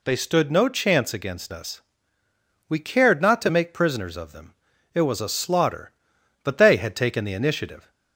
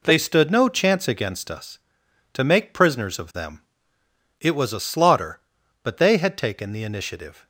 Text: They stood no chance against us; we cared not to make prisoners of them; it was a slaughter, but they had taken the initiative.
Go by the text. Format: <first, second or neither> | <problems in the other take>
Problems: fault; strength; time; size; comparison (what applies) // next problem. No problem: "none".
first | skips "we cared not"; at 2.0 s